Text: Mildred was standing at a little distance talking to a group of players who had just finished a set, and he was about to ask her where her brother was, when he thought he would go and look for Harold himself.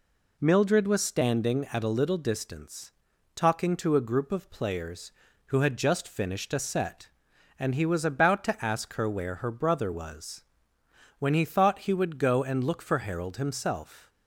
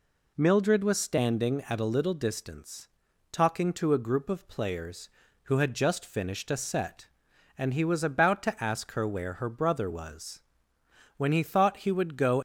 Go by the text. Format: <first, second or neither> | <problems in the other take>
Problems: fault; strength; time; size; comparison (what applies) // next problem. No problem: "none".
first | pauses between "distance" and "talking"; at 2.8 s; 0.42 s long; also in the first // stops before "and look for Harold himself"; at 12.3 s